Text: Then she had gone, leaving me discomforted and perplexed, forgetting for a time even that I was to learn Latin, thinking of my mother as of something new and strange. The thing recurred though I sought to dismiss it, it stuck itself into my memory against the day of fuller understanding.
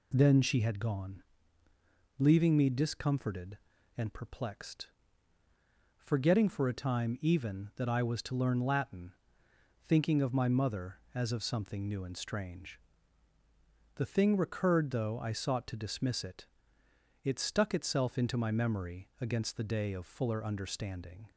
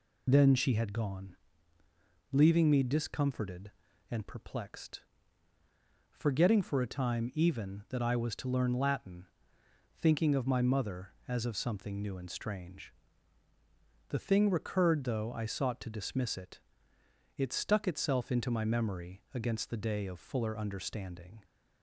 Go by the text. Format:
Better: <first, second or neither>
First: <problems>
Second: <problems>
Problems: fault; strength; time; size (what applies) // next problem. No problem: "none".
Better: first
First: none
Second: loses the start of "Then"; at 0.2 s; 30 ms